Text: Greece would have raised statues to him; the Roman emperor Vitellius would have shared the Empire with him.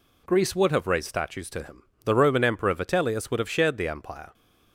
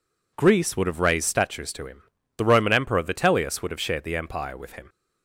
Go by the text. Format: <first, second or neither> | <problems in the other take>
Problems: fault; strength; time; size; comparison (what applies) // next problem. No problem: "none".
second | stops before "with him"; at 4.3 s